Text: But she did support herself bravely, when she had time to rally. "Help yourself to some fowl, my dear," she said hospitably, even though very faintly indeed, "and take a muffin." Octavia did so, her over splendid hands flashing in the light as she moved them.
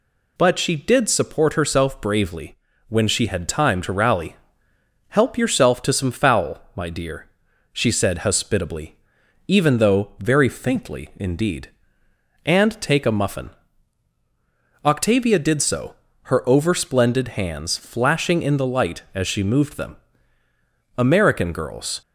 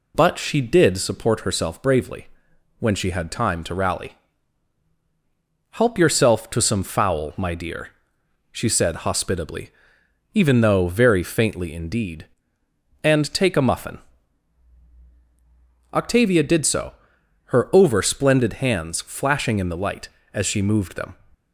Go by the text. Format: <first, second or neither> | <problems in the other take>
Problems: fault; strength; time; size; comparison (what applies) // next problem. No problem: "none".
second | goes on to say "American girls"; noticeable; from 20.9 s on; 1.0 s long